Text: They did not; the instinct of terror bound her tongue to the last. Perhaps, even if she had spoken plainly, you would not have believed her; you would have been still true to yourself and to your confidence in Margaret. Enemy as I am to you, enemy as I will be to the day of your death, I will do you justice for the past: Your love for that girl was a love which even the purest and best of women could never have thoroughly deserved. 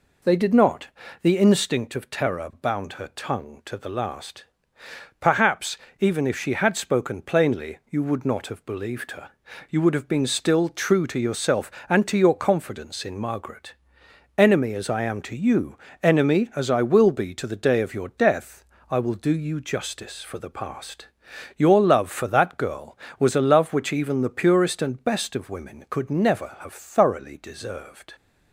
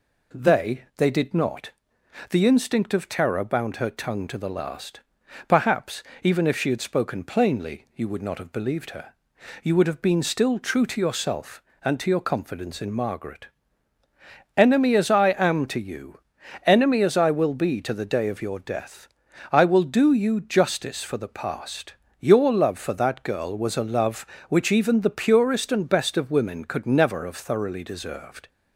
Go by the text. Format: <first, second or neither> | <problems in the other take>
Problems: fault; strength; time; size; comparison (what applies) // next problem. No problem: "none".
first | says "They" twice; at 0.9 s